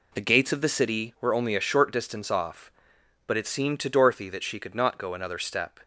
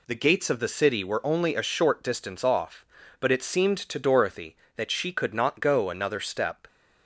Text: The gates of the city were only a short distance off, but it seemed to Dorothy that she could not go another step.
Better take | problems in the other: neither | none

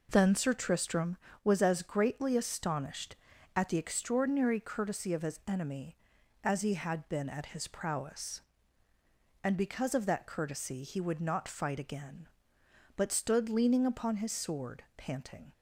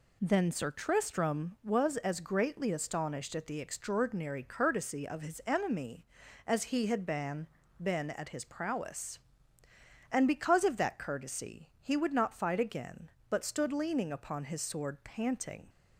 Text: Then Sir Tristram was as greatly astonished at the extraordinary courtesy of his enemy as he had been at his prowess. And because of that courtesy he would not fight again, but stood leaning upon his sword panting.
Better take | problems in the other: first | says "been" twice; at 7.8 s

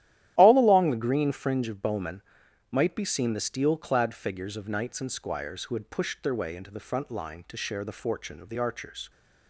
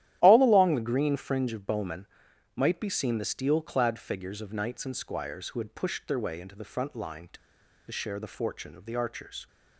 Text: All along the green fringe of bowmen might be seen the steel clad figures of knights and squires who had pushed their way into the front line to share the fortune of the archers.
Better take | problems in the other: first | starts louder than the rest; strong; until 1.2 s; 12.5 dB; strong in the first // pauses between "bowmen" and "might"; noticeable; at 2.0 s; 0.48 s long; noticeable in the first // pauses between "to" and "share"; noticeable; at 7.3 s; 0.53 s long

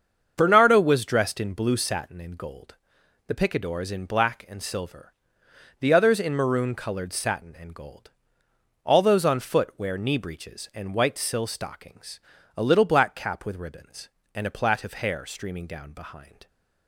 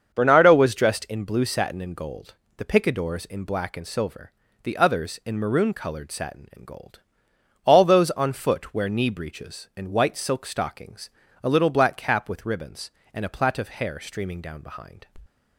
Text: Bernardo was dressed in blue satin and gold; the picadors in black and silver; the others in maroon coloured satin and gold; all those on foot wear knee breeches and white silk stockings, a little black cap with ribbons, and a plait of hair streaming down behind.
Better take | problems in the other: second | starts louder than the rest; until 1.3 s; 7 dB; also in the second // says "sill" for "silk"; at 11.1 s

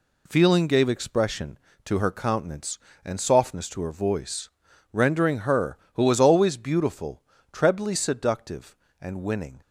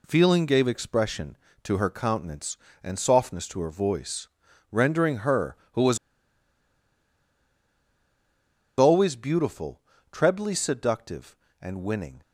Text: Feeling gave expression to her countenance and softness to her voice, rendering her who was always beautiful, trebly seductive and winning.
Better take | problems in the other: first | pauses between "was" and "always"; strong; at 5.9 s; 2.8 s long

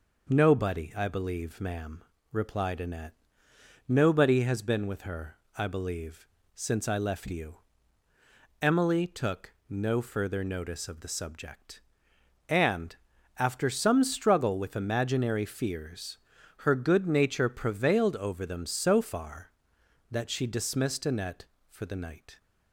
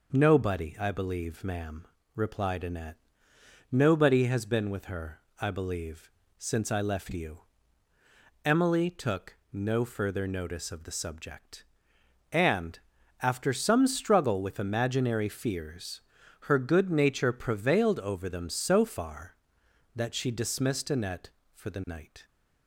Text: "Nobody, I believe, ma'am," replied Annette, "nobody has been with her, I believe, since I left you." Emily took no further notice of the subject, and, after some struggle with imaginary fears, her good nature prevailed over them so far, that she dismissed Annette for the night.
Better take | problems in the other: neither | pauses between "took" and "no"; slight; the same in both

